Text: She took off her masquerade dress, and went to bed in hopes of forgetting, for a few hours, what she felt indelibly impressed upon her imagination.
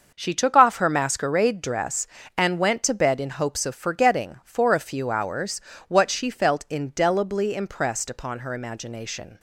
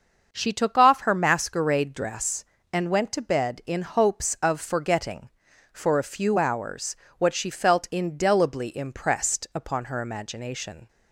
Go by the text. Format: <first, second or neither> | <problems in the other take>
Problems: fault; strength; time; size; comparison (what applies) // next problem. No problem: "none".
neither | starts louder than the rest; the same in both